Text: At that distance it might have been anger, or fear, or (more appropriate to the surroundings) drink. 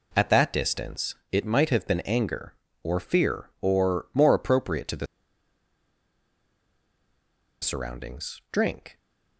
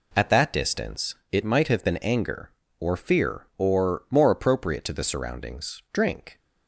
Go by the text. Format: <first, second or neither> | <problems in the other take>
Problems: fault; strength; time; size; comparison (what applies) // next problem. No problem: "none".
second | pauses between "distance" and "it"; slight; at 1.1 s; 0.16 s long; slight in the second // pauses between "the" and "surroundings"; strong; at 5.0 s; 2.5 s long